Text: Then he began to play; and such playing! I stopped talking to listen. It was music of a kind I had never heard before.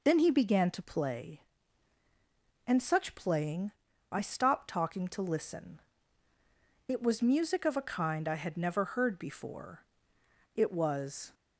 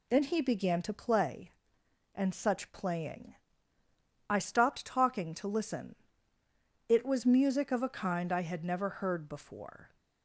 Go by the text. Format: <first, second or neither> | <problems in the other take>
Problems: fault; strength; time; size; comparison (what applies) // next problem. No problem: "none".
second | goes on to say "It was"; noticeable; from 10.5 s on; 0.78 s long